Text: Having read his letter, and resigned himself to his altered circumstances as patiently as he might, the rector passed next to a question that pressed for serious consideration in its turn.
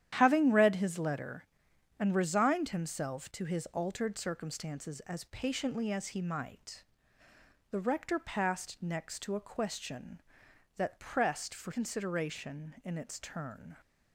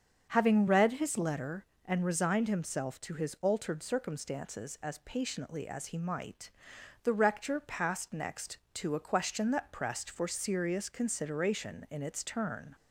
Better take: second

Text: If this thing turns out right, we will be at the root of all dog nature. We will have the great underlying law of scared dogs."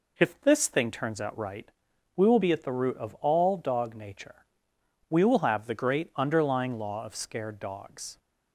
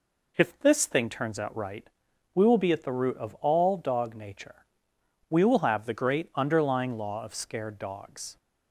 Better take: neither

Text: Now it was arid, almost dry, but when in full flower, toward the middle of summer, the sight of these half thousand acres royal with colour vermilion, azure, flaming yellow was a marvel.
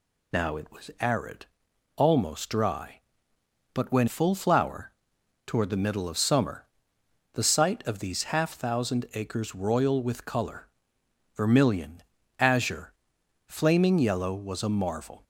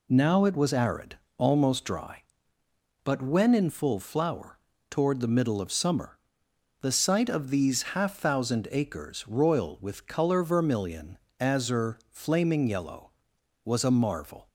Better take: second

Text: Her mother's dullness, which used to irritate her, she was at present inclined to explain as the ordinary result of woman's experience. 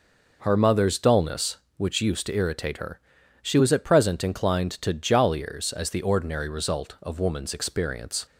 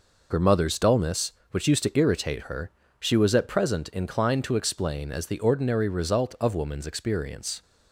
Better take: second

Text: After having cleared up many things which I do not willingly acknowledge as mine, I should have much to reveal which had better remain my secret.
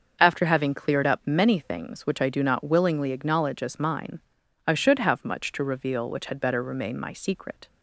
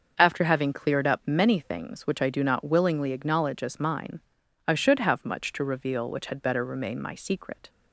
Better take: neither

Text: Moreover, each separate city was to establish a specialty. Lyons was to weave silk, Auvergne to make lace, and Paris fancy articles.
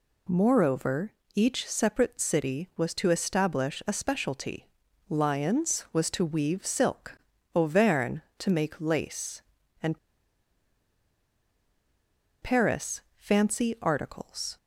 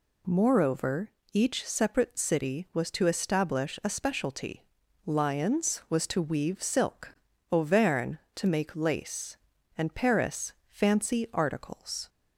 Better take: second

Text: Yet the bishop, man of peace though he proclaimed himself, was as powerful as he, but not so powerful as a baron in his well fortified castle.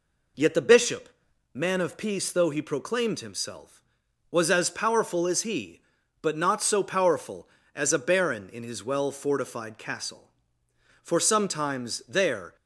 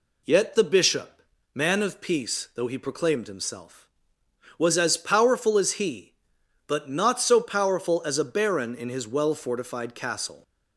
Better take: second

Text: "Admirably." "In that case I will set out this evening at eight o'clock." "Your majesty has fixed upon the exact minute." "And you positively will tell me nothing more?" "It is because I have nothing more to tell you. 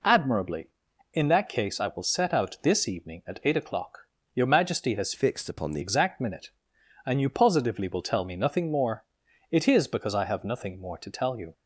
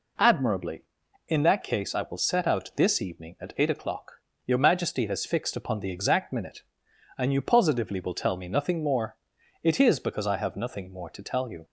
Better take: second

